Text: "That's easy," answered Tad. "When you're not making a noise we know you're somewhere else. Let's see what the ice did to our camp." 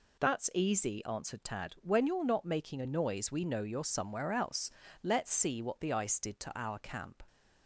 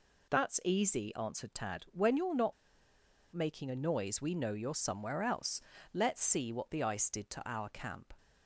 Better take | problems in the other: first | pauses between "not" and "making"; noticeable; at 2.5 s; 0.79 s long

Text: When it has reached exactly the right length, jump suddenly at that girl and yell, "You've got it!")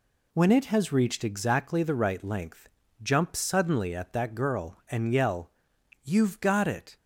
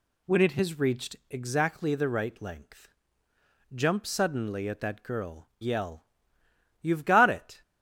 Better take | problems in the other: first | skips "and"; at 5.5 s

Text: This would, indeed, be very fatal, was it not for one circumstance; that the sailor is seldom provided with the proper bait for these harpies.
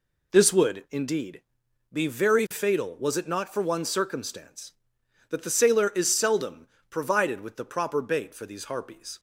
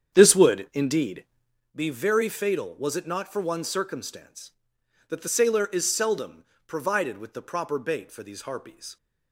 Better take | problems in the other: first | starts louder than the rest; strong; until 1.6 s; 8 dB // pauses between "seldom" and "provided"; slight; at 6.4 s; 0.24 s long; slight in the first

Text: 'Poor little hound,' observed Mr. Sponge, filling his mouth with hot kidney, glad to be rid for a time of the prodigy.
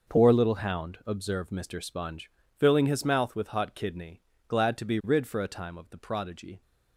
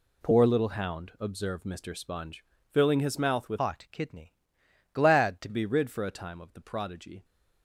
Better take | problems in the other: first | changes voice from "hot" to "to"; from 3.5 to 5.4 s; 1.9 s long

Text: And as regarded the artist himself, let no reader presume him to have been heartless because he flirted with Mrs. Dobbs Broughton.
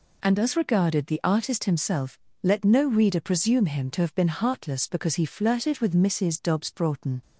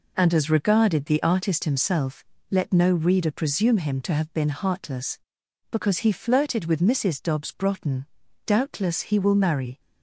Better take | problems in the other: first | goes on to say "Doubtless he will marry"; from 8.4 s on; 1.3 s long

